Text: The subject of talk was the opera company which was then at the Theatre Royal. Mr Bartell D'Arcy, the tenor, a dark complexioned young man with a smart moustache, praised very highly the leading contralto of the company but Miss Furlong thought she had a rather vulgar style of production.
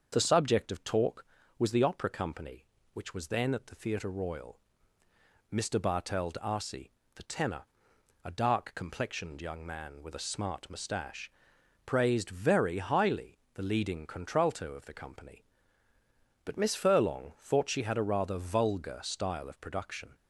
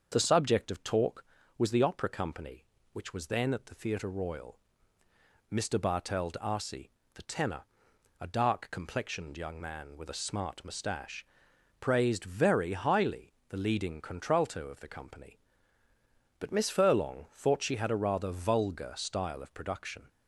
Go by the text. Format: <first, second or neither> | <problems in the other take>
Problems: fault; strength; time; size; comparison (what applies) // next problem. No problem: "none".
neither | starts louder than the rest; the same in both // pauses between "highly" and "the"; slight; the same in both